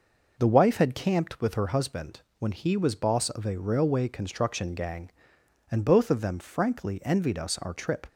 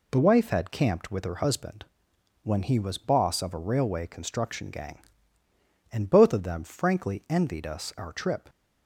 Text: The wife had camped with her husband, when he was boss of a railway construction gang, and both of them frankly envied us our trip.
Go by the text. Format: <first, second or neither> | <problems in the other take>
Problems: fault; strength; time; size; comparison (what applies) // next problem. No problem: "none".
neither | none